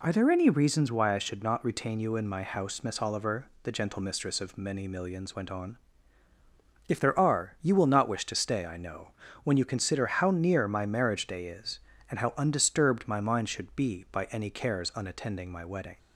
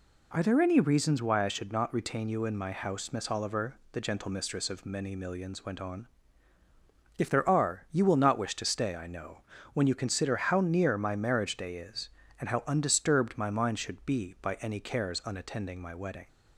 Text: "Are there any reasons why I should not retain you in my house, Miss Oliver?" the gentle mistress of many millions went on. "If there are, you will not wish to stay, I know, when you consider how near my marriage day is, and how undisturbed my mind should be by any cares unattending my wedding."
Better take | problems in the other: neither | none

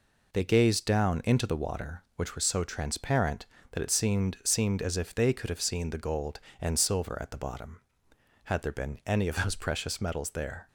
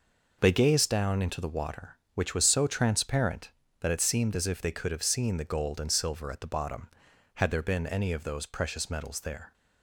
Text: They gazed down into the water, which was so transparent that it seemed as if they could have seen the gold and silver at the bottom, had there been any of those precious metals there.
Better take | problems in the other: second | says "seemed" twice; at 4.4 s

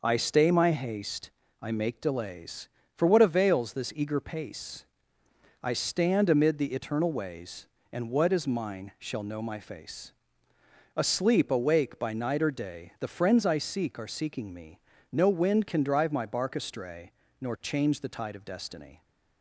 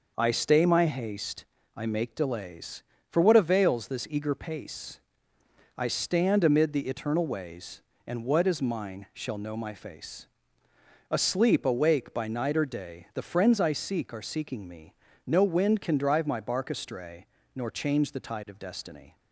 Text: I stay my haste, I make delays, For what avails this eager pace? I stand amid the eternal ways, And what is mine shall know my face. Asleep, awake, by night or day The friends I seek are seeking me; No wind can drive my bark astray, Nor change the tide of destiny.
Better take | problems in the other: neither | none

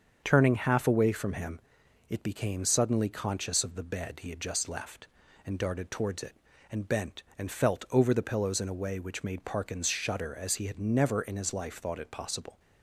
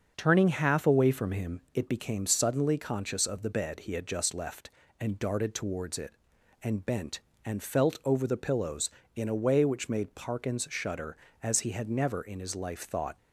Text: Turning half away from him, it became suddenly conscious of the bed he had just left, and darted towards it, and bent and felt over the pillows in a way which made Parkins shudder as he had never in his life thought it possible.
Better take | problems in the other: first | starts louder than the rest; until 1.1 s; 6.5 dB; also in the first // stops before "it possible"; at 13.1 s

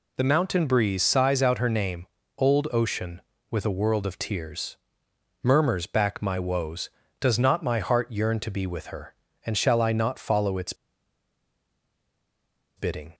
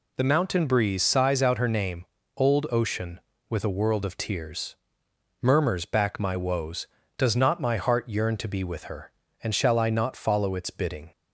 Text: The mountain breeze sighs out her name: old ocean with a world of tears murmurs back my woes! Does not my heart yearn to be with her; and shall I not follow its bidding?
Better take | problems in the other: second | pauses between "tears" and "murmurs"; noticeable; at 4.7 s; 0.66 s long; noticeable in the second // pauses between "its" and "bidding"; strong; at 10.7 s; 2.0 s long

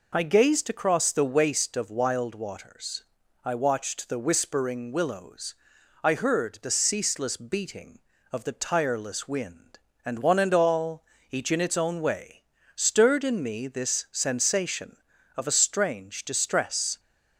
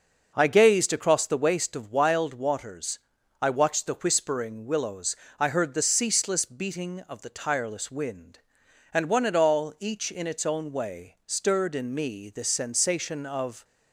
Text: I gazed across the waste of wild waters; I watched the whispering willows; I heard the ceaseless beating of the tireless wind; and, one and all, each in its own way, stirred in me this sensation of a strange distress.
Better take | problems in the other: first | stops before "a strange distress"; at 13.6 s

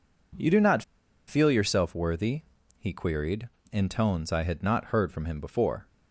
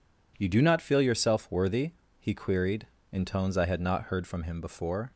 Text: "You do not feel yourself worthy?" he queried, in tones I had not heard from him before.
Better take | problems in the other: second | pauses between "not" and "feel"; noticeable; at 0.8 s; 0.46 s long

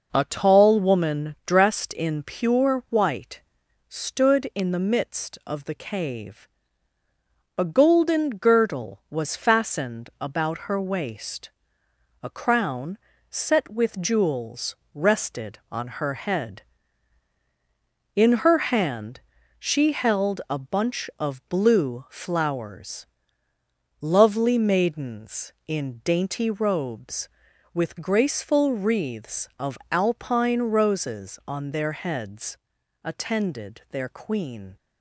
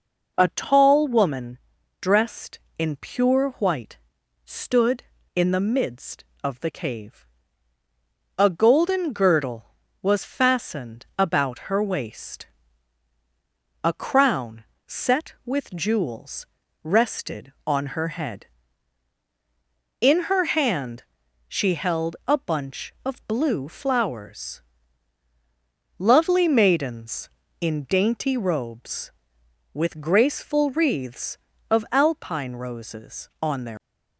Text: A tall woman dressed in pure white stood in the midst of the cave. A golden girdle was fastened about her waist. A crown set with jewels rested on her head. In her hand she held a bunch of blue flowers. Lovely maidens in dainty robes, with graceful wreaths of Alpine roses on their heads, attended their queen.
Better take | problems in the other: first | pauses between "woman" and "dressed"; at 1.5 s; 0.42 s long // pauses between "white" and "stood"; noticeable; at 3.9 s; 0.46 s long; noticeable in the first // pauses between "crown" and "set"; slight; at 14.6 s; 0.24 s long; slight in the first // pauses between "jewels" and "rested"; slight; at 16.4 s; 0.36 s long; slight in the first // pauses between "hand" and "she"; at 21.0 s; 0.42 s long; also in the first // stops before "heads attended their queen"; at 33.7 s

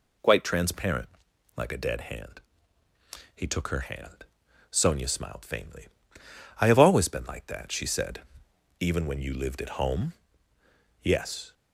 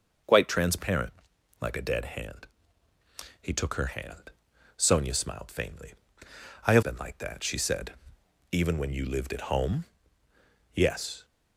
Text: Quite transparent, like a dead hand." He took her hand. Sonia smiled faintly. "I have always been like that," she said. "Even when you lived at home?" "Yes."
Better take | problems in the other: first | skips "always"; at 6.8 s

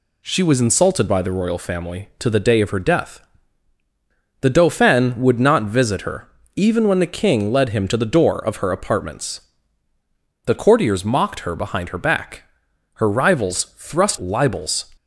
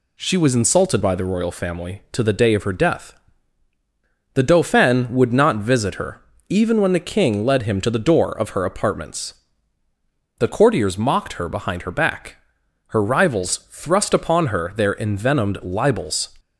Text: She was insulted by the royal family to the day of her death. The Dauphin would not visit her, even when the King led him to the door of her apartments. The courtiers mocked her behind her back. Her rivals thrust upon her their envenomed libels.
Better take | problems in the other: second | skips "upon her their envenomed"; at 14.1 s

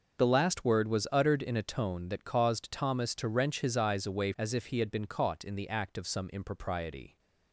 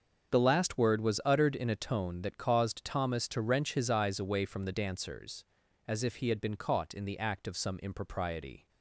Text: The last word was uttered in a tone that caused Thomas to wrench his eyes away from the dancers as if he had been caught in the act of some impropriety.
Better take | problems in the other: second | starts louder than the rest; until 1.2 s; 6.5 dB; also in the second // skips "from the dancers"; at 4.3 s

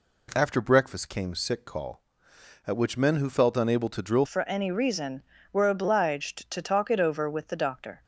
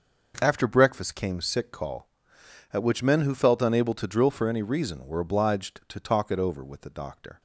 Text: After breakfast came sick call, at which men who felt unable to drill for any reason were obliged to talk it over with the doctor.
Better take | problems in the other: second | changes voice at "for"; from 4.2 s on; 3.8 s long

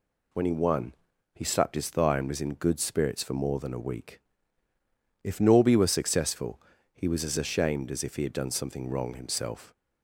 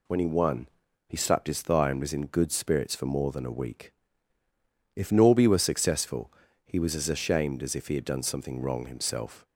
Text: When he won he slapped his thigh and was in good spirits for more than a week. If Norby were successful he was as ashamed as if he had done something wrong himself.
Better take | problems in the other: neither | pauses between "won" and "he"; the same in both // pauses between "successful" and "he"; slight; the same in both

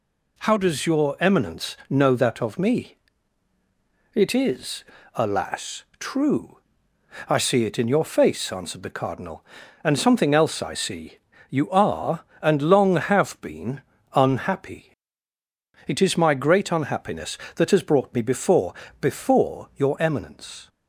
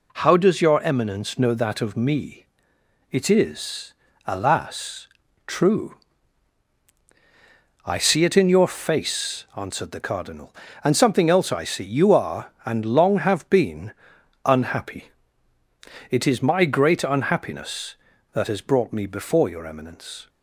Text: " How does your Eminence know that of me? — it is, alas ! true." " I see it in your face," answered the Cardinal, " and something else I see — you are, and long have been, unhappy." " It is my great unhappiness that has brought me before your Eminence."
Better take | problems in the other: second | says "before" twice; at 18.9 s

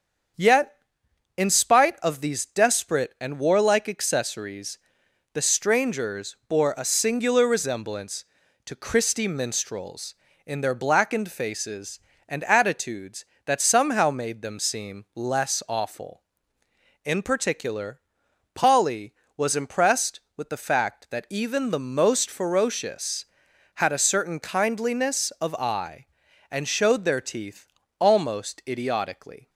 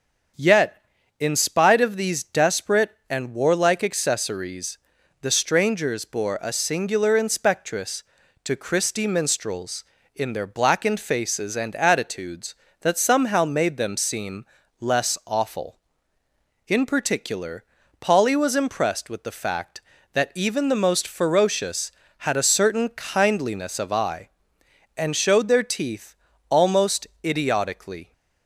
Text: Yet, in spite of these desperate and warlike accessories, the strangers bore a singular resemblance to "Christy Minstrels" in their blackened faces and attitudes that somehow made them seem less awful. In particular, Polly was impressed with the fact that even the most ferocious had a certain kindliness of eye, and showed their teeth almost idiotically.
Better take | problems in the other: first | starts louder than the rest; strong; until 1.7 s; 7 dB; strong in the first // says "inspectress" for "resemblance"; at 7.1 s // pauses between "seem" and "less"; slight; at 14.4 s; 0.36 s long // pauses between "teeth" and "almost"; slight; at 26.1 s; 0.36 s long; slight in the first // pauses between "almost" and "idiotically"; slight; at 27.0 s; 0.18 s long

